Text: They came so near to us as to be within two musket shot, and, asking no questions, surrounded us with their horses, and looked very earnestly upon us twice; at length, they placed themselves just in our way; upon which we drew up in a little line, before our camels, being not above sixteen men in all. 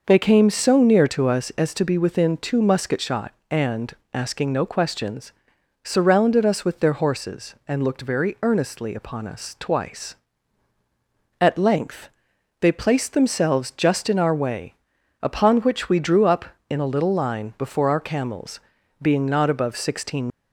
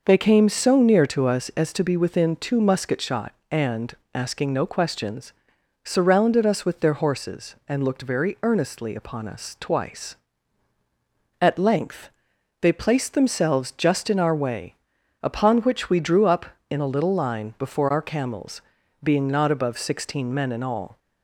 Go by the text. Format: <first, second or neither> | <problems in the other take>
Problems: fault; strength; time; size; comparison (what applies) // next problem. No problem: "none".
second | stops before "men in all"; at 20.3 s